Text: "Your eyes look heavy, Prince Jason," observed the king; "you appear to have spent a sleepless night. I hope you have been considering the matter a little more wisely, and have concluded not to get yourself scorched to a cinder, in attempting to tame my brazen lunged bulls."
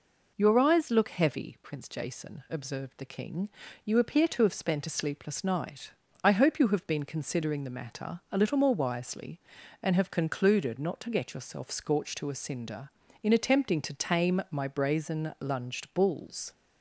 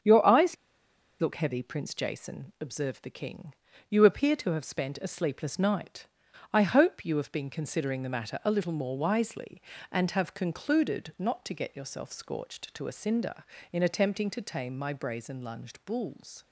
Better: first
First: none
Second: starts louder than the rest; strong; until 1.6 s; 7.5 dB // pauses between "eyes" and "look"; noticeable; at 0.5 s; 0.65 s long

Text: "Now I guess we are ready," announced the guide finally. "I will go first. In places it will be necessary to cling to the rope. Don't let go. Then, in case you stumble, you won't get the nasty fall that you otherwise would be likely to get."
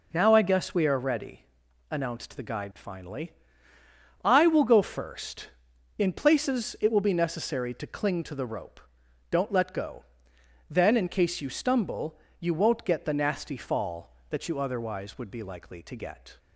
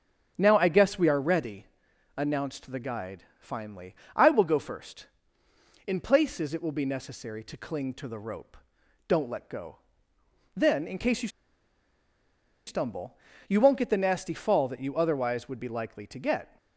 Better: first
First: none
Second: starts louder than the rest; until 1.3 s; 7 dB // pauses between "guide" and "finally"; slight; at 3.2 s; 0.16 s long // pauses between "you" and "stumble"; strong; at 11.2 s; 1.3 s long

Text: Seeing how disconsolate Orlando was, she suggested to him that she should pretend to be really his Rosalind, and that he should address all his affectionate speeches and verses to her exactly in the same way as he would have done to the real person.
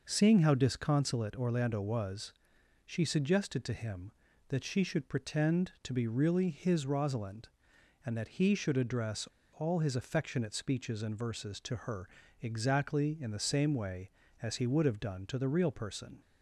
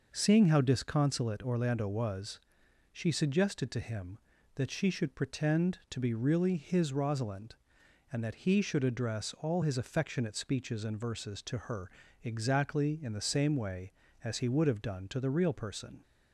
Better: second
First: pauses between "address" and "all"; slight; at 9.2 s; 0.29 s long // pauses between "her" and "exactly"; slight; at 12.0 s; 0.32 s long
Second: pauses between "her" and "exactly"; slight; at 11.9 s; 0.32 s long

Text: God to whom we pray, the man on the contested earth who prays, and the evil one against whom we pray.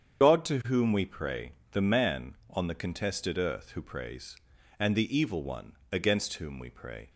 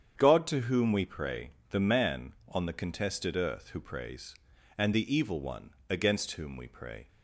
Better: second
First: loses the start of "God"; at 0.2 s; 55 ms // starts louder than the rest; strong; until 1.2 s; 7.5 dB // pauses between "one" and "against"; slight; at 5.7 s; 0.18 s long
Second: starts louder than the rest; strong; until 1.1 s; 8 dB // pauses between "one" and "against"; slight; at 5.7 s; 0.18 s long

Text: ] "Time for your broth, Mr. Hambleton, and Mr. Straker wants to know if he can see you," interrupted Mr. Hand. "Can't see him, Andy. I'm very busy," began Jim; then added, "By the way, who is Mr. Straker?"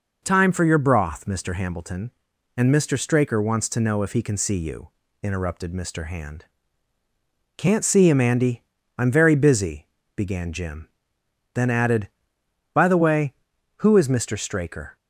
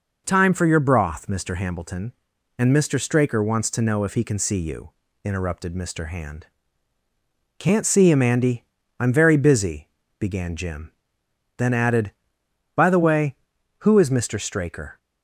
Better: neither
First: none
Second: none

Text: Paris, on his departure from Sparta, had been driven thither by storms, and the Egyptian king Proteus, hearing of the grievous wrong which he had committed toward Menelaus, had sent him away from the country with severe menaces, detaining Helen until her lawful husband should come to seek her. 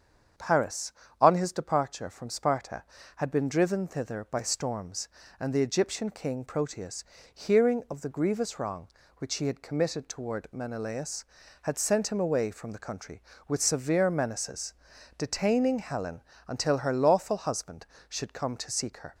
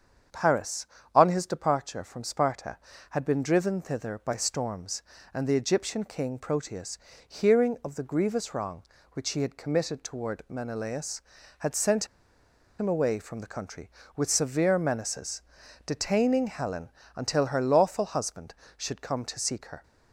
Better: first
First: starts louder than the rest; strong; until 1.6 s; 7.5 dB // pauses between "Helen" and "until"; slight; at 16.2 s; 0.28 s long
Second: starts louder than the rest; strong; until 1.5 s; 7.5 dB // pauses between "sent" and "him"; noticeable; at 12.0 s; 0.73 s long // pauses between "Helen" and "until"; slight; at 16.8 s; 0.28 s long

